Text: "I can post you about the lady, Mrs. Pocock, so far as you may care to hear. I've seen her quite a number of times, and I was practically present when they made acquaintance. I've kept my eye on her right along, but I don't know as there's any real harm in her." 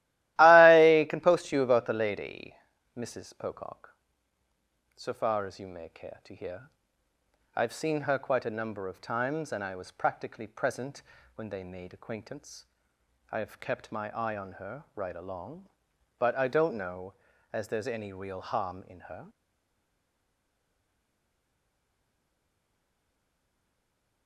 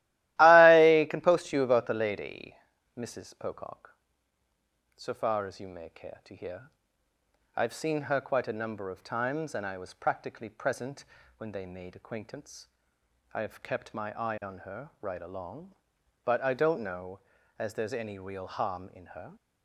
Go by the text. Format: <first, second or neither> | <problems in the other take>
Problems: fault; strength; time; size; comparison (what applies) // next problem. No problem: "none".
second | starts louder than the rest; strong; until 1.4 s; 16 dB; strong in the second // pauses between "present" and "when"; slight; at 11.0 s; 0.34 s long; slight in the second // stays silent after the last word; strong; from 19.2 s on; 5.0 s long